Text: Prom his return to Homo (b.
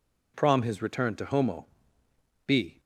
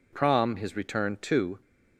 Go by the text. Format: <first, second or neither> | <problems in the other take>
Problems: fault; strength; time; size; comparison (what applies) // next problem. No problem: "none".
first | stops before "Homo b"; at 1.6 s